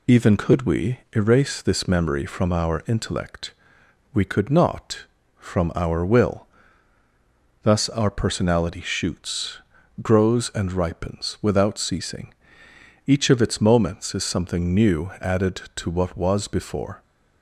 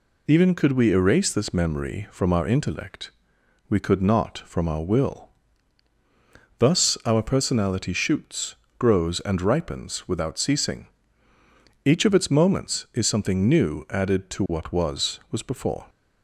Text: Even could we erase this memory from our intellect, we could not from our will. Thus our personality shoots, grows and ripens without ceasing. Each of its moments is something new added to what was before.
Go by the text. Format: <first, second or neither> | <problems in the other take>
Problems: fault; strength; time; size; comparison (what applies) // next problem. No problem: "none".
first | says "was" twice; at 15.3 s